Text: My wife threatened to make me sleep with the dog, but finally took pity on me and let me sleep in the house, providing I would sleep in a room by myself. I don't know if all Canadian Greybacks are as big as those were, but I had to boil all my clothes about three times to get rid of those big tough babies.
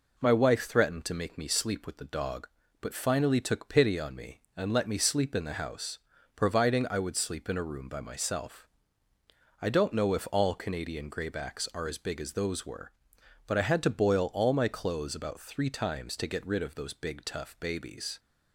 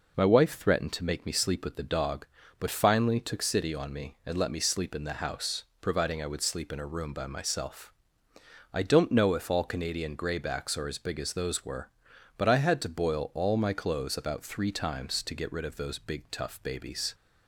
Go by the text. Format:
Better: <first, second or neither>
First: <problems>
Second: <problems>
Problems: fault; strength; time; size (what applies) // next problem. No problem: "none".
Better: first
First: none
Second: says "city" for "pity"; at 3.4 s